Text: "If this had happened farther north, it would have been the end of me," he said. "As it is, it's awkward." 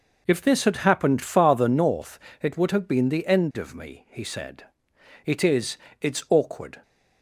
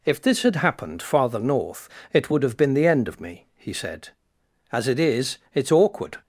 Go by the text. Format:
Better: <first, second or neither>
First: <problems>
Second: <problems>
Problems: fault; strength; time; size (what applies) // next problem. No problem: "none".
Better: second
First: skips "As"; at 4.9 s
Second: none